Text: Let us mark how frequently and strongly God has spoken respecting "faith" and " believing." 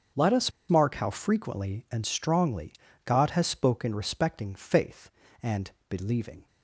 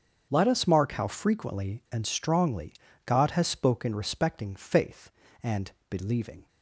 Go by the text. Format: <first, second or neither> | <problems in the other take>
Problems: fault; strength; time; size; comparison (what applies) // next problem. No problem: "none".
second | starts louder than the rest; strong; until 1.3 s; 7.5 dB; strong in the second // pauses between "us" and "mark"; slight; at 0.5 s; 0.17 s long // pauses between "strongly" and "God"; slight; at 2.7 s; 0.32 s long; slight in the second